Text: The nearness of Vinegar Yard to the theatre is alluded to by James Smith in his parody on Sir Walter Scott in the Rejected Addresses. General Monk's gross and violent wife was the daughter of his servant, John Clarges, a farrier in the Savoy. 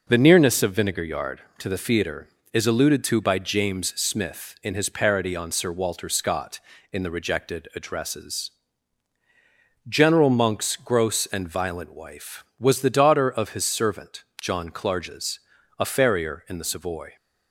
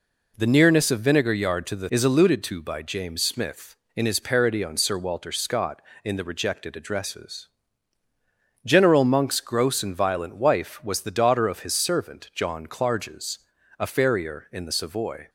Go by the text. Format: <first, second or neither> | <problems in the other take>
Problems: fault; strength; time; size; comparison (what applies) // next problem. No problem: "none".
first | skips "theatre"; at 1.8 s